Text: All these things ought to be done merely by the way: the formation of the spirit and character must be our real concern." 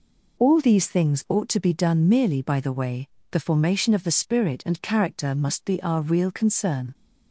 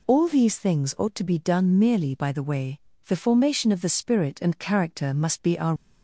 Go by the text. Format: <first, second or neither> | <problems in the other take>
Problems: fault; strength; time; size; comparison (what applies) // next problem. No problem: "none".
first | stops before "real concern"; at 5.7 s